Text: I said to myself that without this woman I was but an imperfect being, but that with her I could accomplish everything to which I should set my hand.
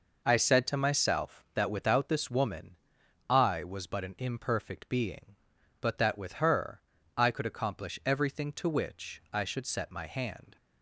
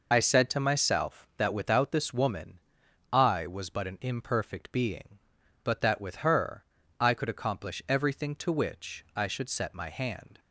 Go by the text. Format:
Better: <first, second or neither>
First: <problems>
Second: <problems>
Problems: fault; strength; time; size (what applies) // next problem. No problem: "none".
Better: first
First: pauses between "woman" and "I"; noticeable; at 2.7 s; 0.54 s long // pauses between "her" and "I"; slight; at 6.8 s; 0.34 s long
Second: loses the start of "I"; at 0.1 s; 40 ms // pauses between "woman" and "I"; noticeable; at 2.5 s; 0.54 s long // pauses between "her" and "I"; slight; at 6.6 s; 0.34 s long